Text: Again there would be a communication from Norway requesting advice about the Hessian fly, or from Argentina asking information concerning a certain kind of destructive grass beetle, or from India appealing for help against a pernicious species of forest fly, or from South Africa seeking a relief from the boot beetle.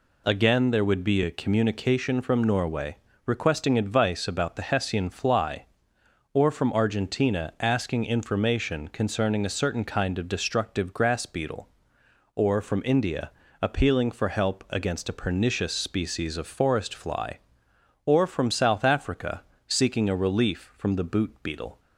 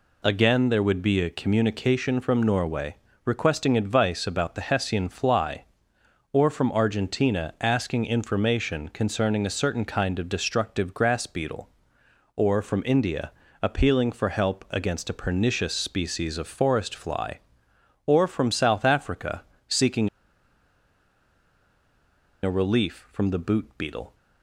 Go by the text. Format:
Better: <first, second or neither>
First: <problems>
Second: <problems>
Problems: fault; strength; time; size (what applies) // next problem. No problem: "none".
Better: first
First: pauses between "Norway" and "requesting"; slight; at 2.9 s; 0.28 s long // pauses between "India" and "appealing"; slight; at 13.3 s; 0.30 s long // pauses between "Africa" and "seeking"; slight; at 19.4 s; 0.26 s long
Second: pauses between "Norway" and "requesting"; slight; at 2.9 s; 0.28 s long // pauses between "India" and "appealing"; slight; at 13.3 s; 0.30 s long // pauses between "Africa" and "seeking"; slight; at 19.4 s; 0.26 s long // pauses between "seeking" and "a"; strong; at 20.0 s; 2.3 s long